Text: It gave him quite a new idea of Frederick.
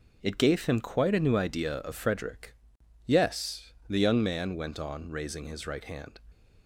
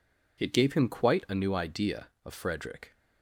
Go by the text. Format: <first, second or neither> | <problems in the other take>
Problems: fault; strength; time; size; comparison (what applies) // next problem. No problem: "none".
second | goes on to say "Yes the young man went on raising his right hand"; strong; from 3.0 s on; 3.1 s long